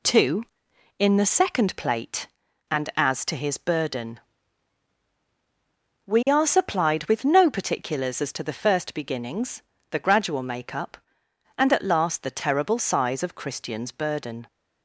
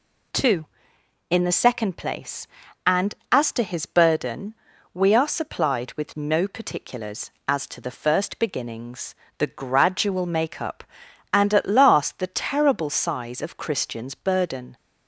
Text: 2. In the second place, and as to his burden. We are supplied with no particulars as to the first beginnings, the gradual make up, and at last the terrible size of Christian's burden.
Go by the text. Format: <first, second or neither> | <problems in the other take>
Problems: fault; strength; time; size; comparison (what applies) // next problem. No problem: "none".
second | says "plate" for "place"; at 1.7 s